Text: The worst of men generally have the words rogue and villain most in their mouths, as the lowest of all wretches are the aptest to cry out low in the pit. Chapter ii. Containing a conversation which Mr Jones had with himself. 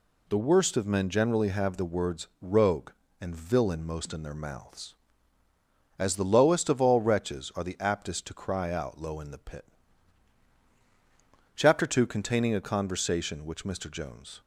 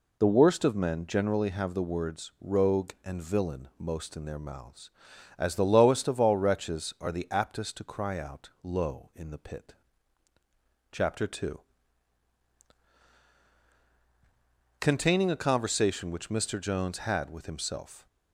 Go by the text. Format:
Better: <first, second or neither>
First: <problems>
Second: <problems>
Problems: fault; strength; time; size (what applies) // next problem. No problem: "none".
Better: second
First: stops before "had with himself"; at 14.4 s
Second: none